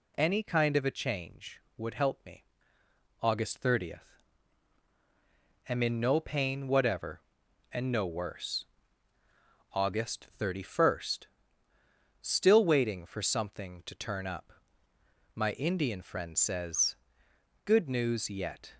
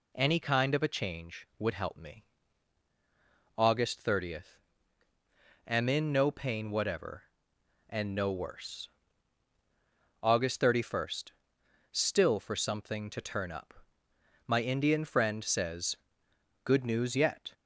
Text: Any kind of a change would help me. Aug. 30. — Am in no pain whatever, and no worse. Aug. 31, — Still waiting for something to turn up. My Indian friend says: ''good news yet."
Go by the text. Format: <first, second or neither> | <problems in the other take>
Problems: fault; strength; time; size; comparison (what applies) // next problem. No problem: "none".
first | skips "waiting"; at 12.3 s